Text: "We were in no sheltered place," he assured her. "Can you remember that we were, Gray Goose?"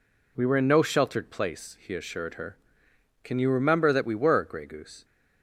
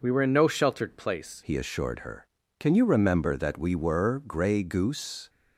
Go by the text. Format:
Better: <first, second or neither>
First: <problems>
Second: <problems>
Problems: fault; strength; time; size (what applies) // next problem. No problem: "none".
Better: first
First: none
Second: changes voice at "he"; from 1.4 s on; 3.8 s long